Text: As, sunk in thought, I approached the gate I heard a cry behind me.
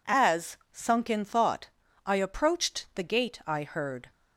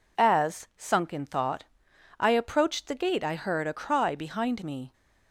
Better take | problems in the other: second | stops before "a cry behind me"; at 4.1 s

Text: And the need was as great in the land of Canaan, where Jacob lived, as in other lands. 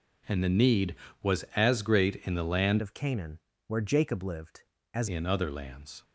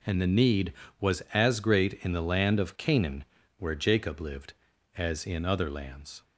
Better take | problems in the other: second | changes voice from "of" to "as"; from 2.8 to 5.0 s; 2.2 s long

